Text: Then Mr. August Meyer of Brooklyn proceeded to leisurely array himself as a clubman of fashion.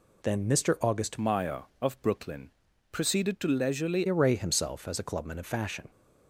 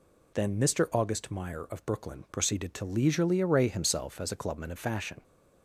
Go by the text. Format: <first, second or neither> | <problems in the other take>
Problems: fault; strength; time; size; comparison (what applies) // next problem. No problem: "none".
second | changes voice from "Meyer" to "leisurely"; from 1.1 to 4.0 s; 2.9 s long // pauses between "Brooklyn" and "proceeded"; at 2.4 s; 0.40 s long